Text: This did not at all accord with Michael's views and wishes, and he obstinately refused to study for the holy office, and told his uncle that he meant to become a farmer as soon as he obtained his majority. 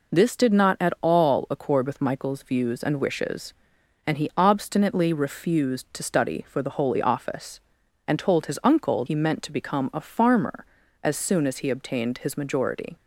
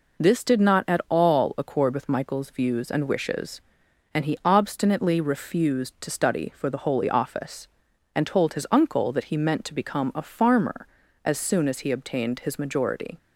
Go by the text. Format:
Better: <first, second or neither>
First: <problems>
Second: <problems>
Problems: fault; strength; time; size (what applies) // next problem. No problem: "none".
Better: second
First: skips "that"; at 9.0 s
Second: none